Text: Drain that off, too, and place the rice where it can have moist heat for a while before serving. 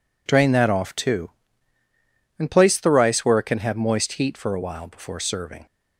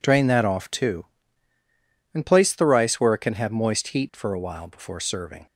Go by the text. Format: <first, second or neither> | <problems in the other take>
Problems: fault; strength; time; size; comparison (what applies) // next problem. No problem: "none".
neither | none